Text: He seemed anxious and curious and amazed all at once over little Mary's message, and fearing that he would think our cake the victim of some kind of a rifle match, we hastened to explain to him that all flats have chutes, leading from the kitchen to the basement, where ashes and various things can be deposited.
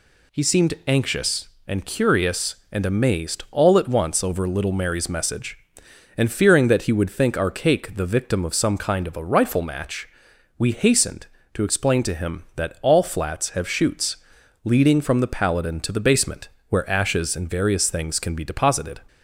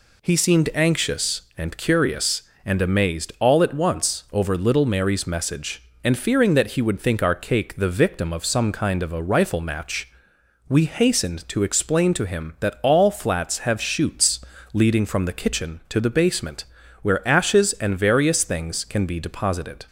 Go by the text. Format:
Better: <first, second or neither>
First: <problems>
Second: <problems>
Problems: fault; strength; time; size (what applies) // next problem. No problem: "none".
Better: second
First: says "paladin" for "kitchen"; at 15.2 s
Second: none